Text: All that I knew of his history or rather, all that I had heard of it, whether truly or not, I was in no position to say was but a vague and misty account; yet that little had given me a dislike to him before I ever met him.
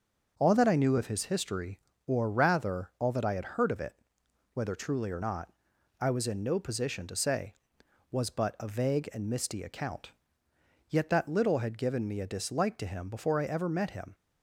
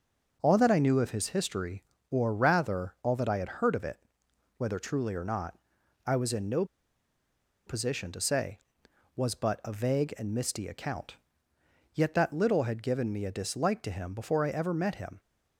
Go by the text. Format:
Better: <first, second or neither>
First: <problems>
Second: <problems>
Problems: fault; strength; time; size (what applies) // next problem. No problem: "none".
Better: first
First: none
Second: pauses between "no" and "position"; at 6.6 s; 1.0 s long